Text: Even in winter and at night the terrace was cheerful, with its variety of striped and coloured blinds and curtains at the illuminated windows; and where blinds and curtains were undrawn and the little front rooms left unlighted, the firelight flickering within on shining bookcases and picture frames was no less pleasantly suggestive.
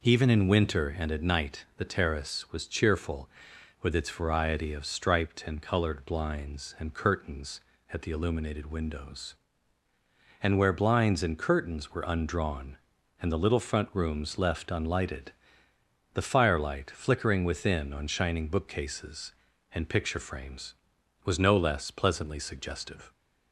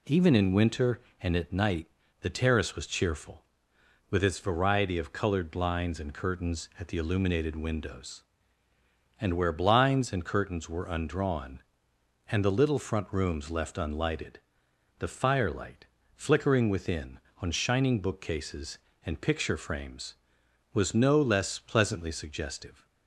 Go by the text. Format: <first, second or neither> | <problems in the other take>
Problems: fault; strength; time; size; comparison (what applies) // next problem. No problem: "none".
first | pauses between "night" and "the"; slight; at 1.8 s; 0.34 s long // skips "striped and"; at 5.1 s // pauses between "firelight" and "flickering"; slight; at 15.8 s; 0.30 s long